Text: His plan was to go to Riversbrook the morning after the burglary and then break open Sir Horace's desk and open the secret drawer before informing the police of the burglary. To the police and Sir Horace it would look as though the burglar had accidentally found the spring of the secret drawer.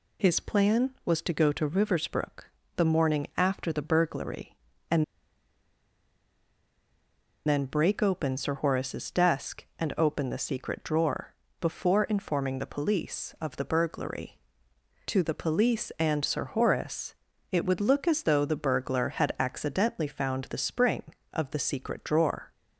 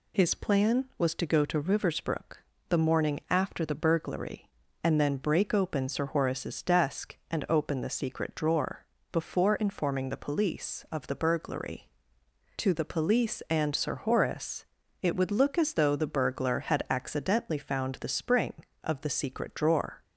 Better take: second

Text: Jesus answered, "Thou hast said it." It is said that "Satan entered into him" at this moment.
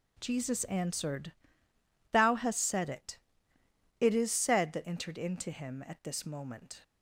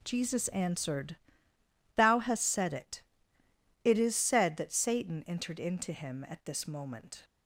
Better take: second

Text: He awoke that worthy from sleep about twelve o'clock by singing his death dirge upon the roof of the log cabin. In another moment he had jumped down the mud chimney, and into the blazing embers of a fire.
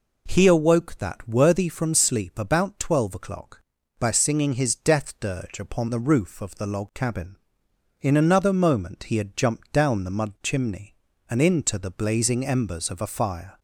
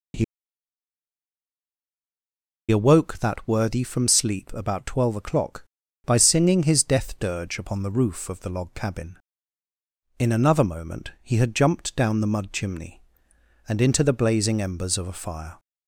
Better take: first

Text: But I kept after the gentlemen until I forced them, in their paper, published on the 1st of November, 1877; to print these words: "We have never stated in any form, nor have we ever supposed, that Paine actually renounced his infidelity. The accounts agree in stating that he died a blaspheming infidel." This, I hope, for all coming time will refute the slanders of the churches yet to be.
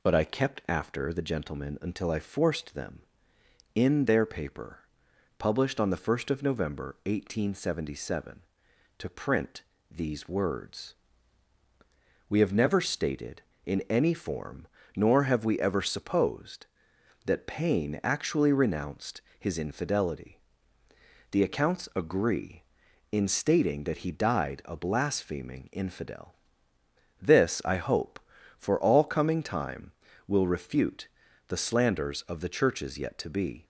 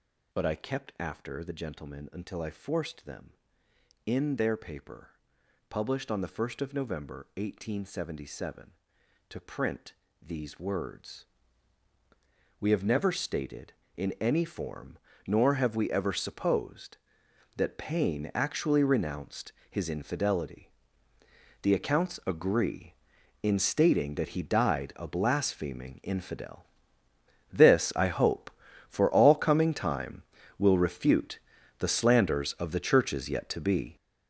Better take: first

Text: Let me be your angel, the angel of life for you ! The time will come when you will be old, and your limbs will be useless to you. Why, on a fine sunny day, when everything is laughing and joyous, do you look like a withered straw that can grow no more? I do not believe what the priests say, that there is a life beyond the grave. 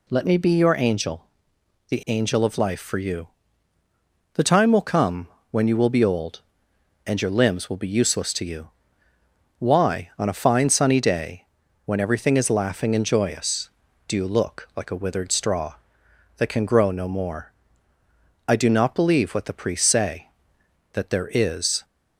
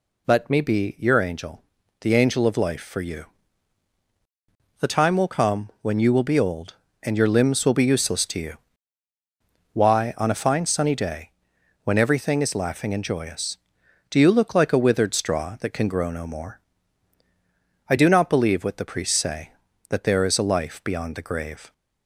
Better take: second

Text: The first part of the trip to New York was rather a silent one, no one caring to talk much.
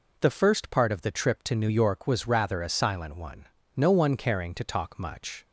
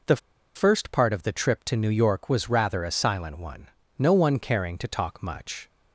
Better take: first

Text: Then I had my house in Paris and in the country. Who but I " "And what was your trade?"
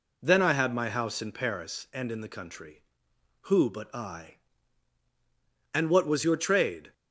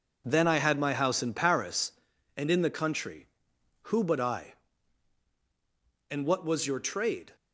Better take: first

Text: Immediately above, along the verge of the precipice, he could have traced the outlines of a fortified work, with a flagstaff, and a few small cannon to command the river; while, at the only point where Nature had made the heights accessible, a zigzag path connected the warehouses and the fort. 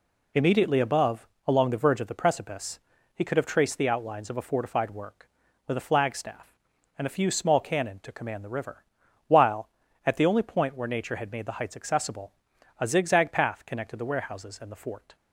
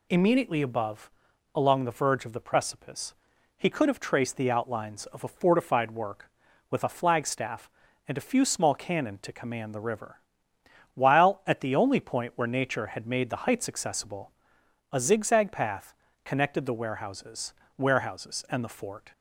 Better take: first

